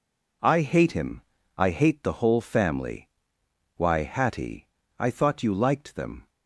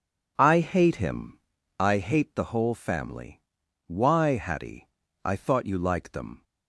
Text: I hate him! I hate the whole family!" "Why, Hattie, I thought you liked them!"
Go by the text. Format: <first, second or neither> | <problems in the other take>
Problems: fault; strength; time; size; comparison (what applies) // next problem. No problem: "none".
neither | none